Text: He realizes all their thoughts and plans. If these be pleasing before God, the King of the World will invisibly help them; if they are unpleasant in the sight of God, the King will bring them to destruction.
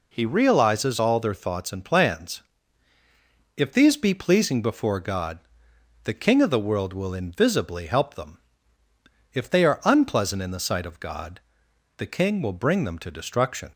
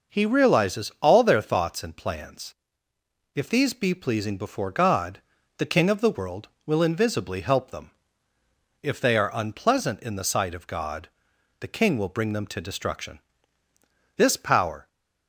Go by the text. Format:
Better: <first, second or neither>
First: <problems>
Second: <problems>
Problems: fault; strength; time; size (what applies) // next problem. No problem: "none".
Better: first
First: none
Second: goes on to say "This power"; noticeable; from 14.1 s on; 0.70 s long